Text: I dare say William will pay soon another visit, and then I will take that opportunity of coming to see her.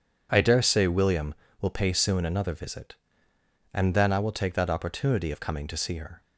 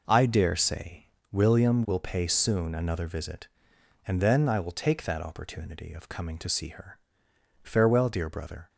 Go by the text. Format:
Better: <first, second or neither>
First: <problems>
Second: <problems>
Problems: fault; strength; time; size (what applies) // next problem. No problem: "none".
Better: first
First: none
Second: pauses between "say" and "William"; slight; at 1.0 s; 0.24 s long // goes on to say "Farewell dear brother"; noticeable; from 7.6 s on; 1.0 s long